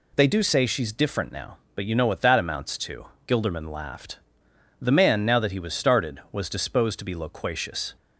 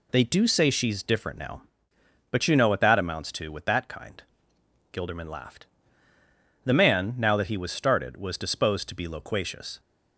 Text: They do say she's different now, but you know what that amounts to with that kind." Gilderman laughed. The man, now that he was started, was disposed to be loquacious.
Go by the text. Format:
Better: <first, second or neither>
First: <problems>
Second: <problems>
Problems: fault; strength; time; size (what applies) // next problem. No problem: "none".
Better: second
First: skips "with that kind"; at 3.1 s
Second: none